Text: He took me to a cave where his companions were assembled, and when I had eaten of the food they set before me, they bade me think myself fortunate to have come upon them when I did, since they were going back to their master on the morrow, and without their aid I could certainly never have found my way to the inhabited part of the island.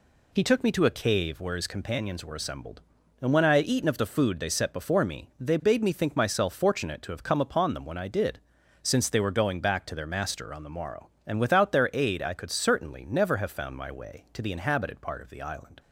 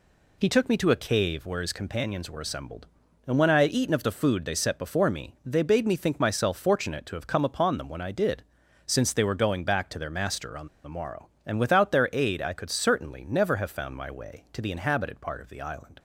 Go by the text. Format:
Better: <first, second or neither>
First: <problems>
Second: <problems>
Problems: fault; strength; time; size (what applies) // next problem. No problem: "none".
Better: first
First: none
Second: pauses between "on" and "the"; slight; at 10.6 s; 0.17 s long